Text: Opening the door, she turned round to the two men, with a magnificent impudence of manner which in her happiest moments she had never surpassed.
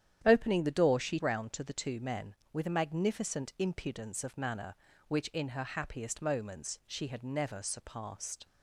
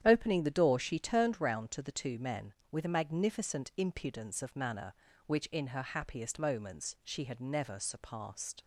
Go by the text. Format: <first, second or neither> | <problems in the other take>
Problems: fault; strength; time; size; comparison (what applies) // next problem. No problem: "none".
second | starts louder than the rest; strong; until 1.2 s; 10 dB; strong in the second // skips "turned"; at 1.1 s